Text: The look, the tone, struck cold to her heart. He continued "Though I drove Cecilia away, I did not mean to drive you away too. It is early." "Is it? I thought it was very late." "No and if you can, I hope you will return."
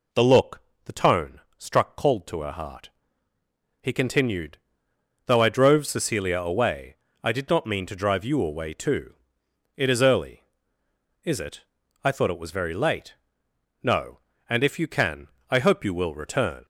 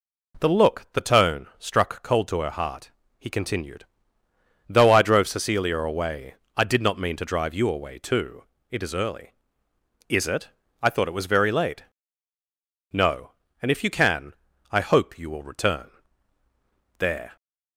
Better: first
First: pauses between "continued" and "Though"; noticeable; at 4.5 s; 0.70 s long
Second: pauses between "continued" and "Though"; noticeable; at 3.8 s; 0.82 s long // goes on to say "There"; slight; from 16.9 s on; 0.38 s long

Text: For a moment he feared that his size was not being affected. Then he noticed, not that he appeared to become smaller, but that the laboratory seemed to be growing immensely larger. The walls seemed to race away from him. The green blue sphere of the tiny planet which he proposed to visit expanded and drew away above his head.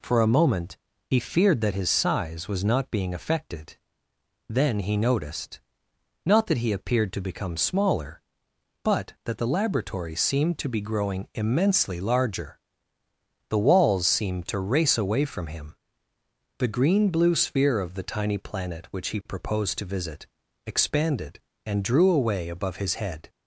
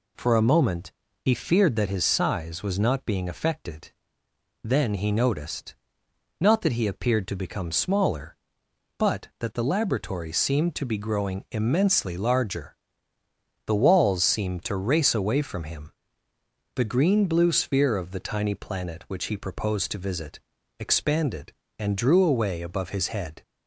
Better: neither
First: pauses between "moment" and "he"; slight; at 0.7 s; 0.32 s long // pauses between "visit" and "expanded"; at 20.2 s; 0.40 s long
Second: pauses between "moment" and "he"; slight; at 0.9 s; 0.32 s long // pauses between "visit" and "expanded"; at 20.4 s; 0.40 s long

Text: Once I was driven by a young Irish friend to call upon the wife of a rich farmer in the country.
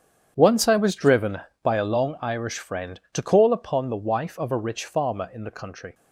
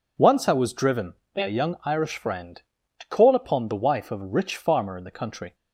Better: second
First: starts louder than the rest; strong; until 1.3 s; 8.5 dB // says "long" for "young"; at 1.8 s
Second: none

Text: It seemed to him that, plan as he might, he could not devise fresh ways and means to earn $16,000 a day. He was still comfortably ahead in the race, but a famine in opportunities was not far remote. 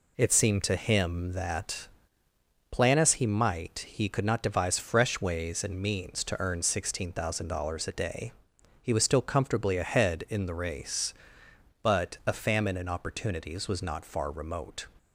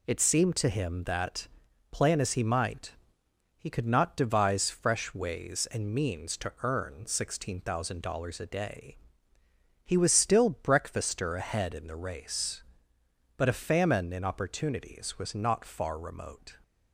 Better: first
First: none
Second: says "breakfaster" for "comfortably"; at 10.6 s

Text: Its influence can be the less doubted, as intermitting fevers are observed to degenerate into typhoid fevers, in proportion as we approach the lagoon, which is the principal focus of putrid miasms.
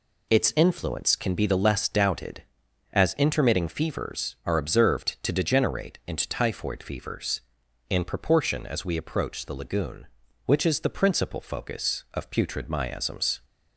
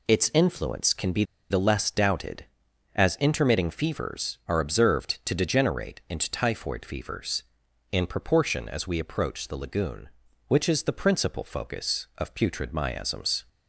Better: first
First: none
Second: pauses between "be" and "the"; slight; at 1.2 s; 0.26 s long

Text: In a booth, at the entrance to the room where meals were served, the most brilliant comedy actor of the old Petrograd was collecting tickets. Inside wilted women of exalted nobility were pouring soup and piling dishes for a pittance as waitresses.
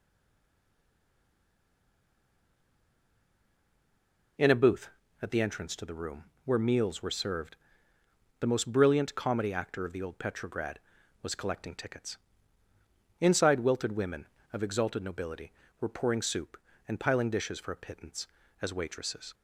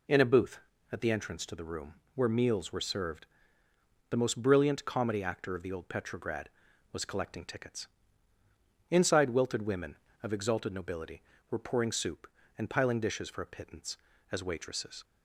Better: second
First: stays silent before the first word; strong; until 4.3 s; 4.3 s long // pauses between "room" and "where"; slight; at 6.2 s; 0.18 s long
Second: pauses between "room" and "where"; slight; at 1.9 s; 0.18 s long

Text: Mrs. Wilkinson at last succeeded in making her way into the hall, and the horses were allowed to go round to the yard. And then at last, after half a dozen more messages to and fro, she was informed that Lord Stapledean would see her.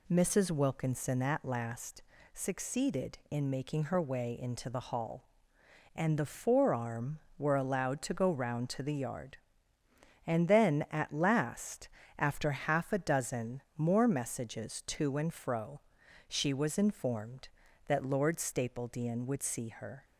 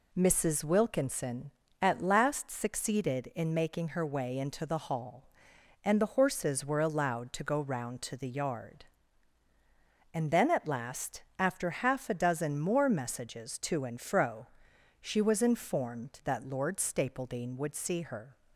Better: second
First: pauses between "last" and "succeeded"; slight; at 2.0 s; 0.28 s long // says "forearm" for "horses"; at 6.2 s // pauses between "dozen" and "more"; slight; at 13.6 s; 0.16 s long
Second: none

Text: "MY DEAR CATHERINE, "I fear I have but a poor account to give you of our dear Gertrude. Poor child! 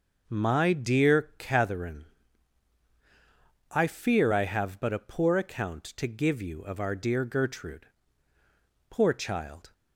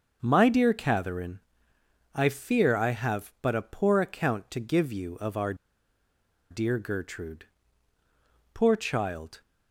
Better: first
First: none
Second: starts louder than the rest; until 1.2 s; 6.5 dB // pauses between "our" and "dear"; noticeable; at 5.5 s; 0.96 s long

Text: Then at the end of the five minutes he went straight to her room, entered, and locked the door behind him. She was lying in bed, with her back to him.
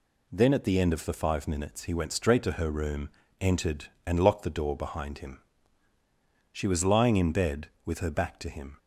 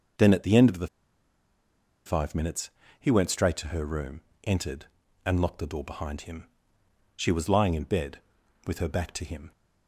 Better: first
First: none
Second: pauses between "the" and "five"; at 0.8 s; 1.1 s long // pauses between "minutes" and "he"; slight; at 2.6 s; 0.30 s long

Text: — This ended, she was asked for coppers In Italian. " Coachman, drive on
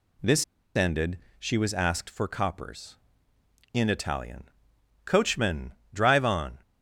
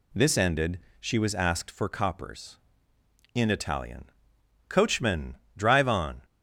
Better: second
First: pauses between "This" and "ended"; slight; at 0.4 s; 0.31 s long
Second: none

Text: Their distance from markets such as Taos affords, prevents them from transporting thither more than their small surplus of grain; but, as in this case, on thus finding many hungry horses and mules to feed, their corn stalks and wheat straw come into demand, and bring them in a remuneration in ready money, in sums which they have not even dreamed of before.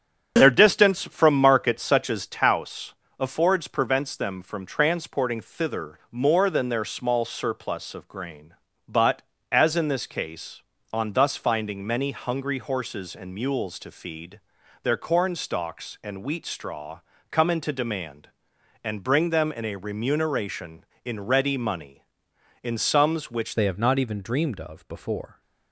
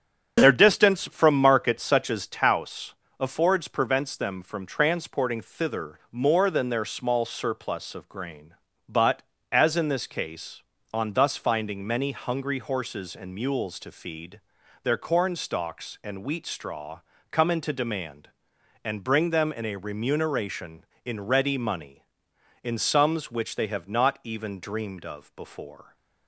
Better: second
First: starts louder than the rest; strong; until 1.3 s; 8 dB // pauses between "Taos" and "affords"; slight; at 2.9 s; 0.26 s long // pauses between "straw" and "come"; slight; at 16.9 s; 0.32 s long // changes voice at "they"; from 23.5 s on; 1.9 s long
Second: starts louder than the rest; strong; until 1.4 s; 8 dB // pauses between "Taos" and "affords"; slight; at 2.9 s; 0.26 s long // pauses between "straw" and "come"; slight; at 16.9 s; 0.32 s long

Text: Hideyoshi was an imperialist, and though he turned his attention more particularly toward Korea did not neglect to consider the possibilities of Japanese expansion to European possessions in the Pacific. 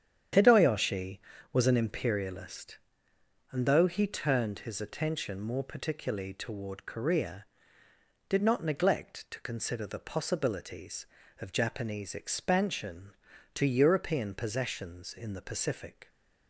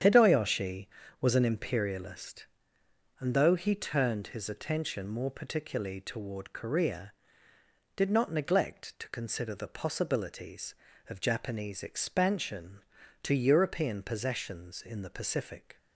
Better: neither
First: starts louder than the rest; strong; until 1.6 s; 9 dB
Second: starts louder than the rest; strong; until 1.3 s; 9 dB

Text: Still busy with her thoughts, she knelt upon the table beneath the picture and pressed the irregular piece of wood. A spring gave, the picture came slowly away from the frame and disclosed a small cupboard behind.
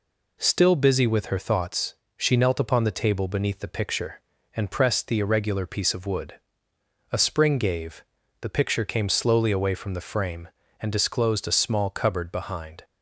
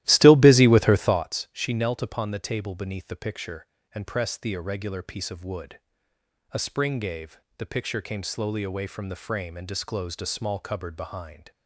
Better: first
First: none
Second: starts louder than the rest; strong; until 1.3 s; 15 dB

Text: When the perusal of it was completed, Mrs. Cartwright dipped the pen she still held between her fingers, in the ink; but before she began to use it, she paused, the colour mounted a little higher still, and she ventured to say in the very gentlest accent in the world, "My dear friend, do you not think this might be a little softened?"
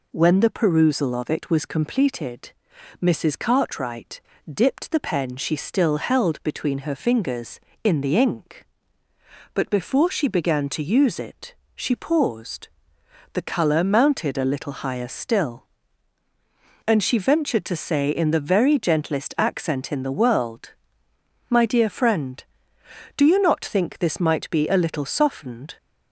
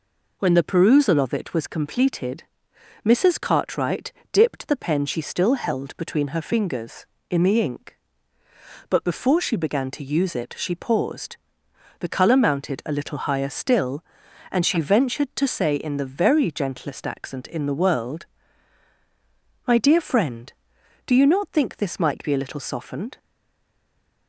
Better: first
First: pauses between "Cartwright" and "dipped"; slight; at 4.1 s; 0.26 s long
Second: pauses between "Cartwright" and "dipped"; slight; at 4.1 s; 0.20 s long // stays silent after the last word; from 23.1 s on; 1.1 s long

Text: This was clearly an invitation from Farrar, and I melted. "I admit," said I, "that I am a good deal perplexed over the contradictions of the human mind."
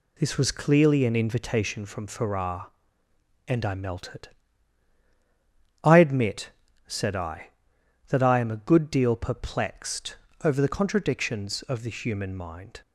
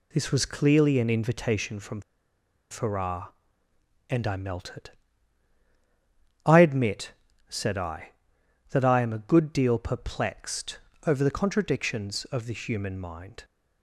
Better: first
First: pauses between "perplexed" and "over"; slight; at 10.1 s; 0.30 s long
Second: pauses between "from" and "Farrar"; noticeable; at 2.0 s; 0.70 s long // pauses between "perplexed" and "over"; slight; at 10.7 s; 0.30 s long

